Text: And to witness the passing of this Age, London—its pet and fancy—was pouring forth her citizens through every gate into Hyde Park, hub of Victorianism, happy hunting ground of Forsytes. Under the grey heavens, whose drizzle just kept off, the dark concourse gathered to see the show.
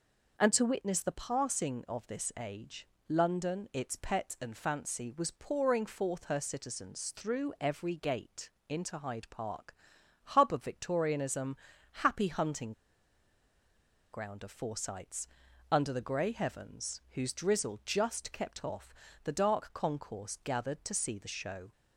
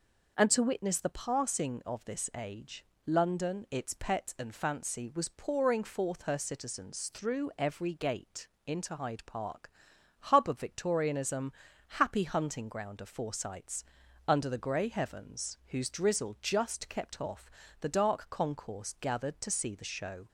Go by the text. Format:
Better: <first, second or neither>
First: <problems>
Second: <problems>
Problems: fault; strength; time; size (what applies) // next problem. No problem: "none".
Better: second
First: pauses between "gate" and "into"; slight; at 8.5 s; 0.18 s long // pauses between "hunting" and "ground"; strong; at 12.7 s; 1.4 s long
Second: pauses between "gate" and "into"; slight; at 8.4 s; 0.18 s long